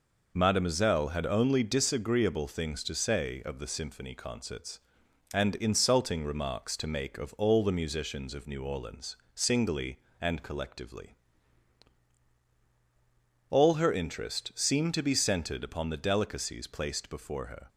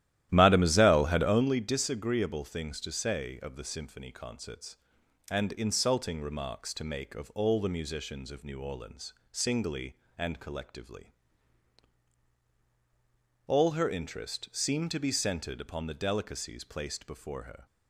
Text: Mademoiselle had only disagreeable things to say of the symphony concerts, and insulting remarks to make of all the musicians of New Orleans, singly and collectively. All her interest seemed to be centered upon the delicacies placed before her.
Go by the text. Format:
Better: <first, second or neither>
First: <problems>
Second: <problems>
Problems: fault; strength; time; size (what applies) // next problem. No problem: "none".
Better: first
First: none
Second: starts louder than the rest; strong; until 1.5 s; 13 dB